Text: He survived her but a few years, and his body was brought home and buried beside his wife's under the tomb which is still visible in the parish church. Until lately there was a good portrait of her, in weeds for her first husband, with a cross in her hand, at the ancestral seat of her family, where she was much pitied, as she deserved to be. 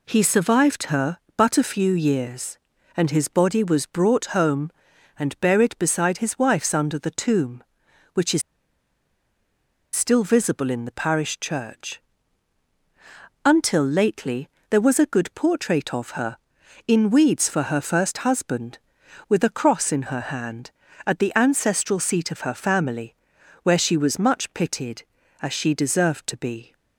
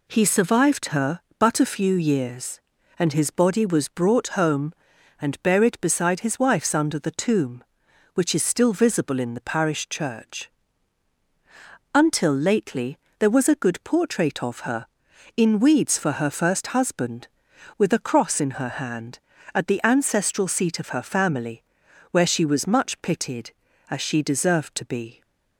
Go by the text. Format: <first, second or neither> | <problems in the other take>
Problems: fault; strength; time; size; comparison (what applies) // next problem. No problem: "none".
second | pauses between "is" and "still"; strong; at 8.4 s; 1.5 s long // pauses between "lately" and "there"; slight; at 14.4 s; 0.22 s long; slight in the second